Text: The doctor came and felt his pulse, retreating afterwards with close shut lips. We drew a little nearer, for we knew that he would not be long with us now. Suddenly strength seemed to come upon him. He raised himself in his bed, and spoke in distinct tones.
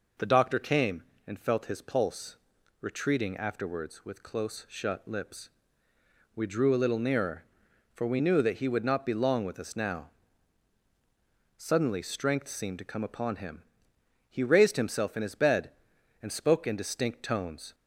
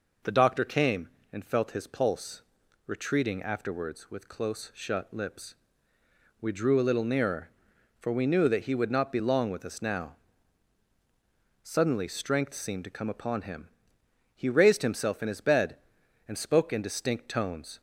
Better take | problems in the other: neither | none

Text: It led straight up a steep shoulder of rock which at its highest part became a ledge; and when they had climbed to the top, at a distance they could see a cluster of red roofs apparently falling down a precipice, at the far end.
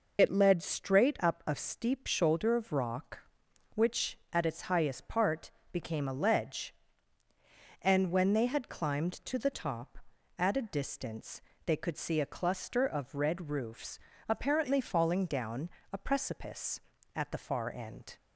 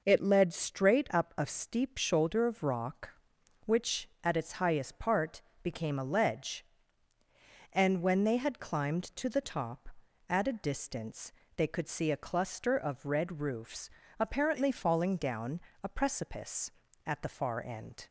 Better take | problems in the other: second | loses the start of "It"; at 0.1 s; 50 ms // pauses between "part" and "became"; slight; at 5.5 s; 0.20 s long; slight in the second // pauses between "distance" and "they"; slight; at 11.3 s; 0.26 s long; slight in the second // pauses between "roofs" and "apparently"; slight; at 13.9 s; 0.28 s long; slight in the second // pauses between "down" and "a"; slight; at 15.6 s; 0.22 s long; slight in the second

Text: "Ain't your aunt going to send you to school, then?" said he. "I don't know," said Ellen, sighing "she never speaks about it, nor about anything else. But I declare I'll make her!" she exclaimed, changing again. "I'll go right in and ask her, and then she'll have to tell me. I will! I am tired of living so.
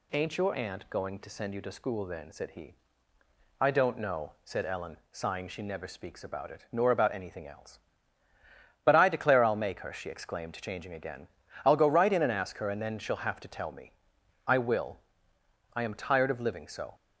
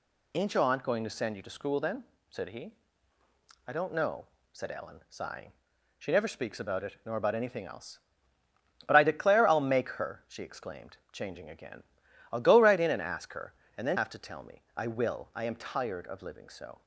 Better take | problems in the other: first | pauses between "sighing" and "she"; at 5.5 s; 0.44 s long // skips "she'll"; at 13.9 s

